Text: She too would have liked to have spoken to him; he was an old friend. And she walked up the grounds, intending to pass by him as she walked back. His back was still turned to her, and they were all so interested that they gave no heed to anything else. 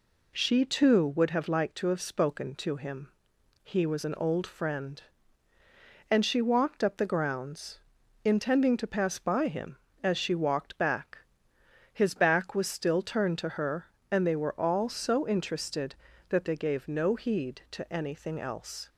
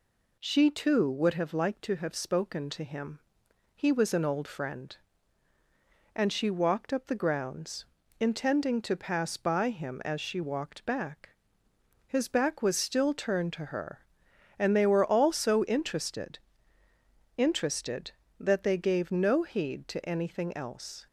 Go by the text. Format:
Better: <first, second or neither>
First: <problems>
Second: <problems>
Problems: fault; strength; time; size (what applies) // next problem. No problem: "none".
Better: first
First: none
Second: says "interested" twice; at 17.3 s